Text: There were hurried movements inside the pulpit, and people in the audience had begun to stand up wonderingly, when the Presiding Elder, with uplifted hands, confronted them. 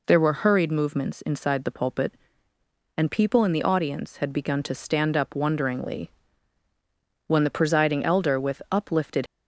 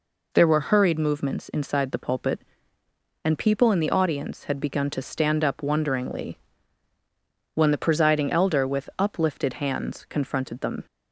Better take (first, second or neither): second